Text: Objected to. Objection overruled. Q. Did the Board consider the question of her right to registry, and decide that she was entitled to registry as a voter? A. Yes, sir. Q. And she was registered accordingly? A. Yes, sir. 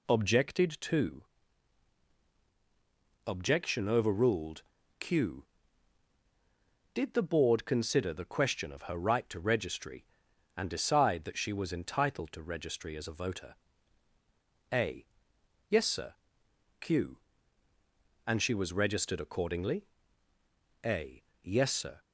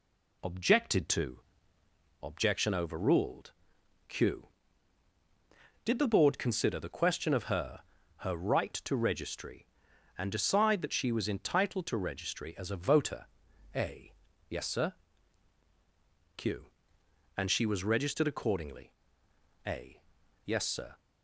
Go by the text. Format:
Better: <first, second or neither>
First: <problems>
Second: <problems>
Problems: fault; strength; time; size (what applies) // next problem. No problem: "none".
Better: first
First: none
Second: says "her" twice; at 8.1 s